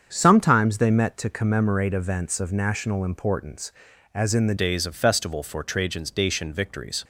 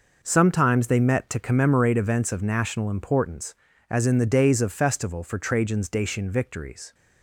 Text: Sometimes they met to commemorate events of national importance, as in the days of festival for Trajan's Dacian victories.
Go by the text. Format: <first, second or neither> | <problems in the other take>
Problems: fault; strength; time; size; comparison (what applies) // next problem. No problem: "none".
second | starts louder than the rest; strong; until 1.1 s; 7 dB // changes voice at "days"; from 4.5 s on; 2.5 s long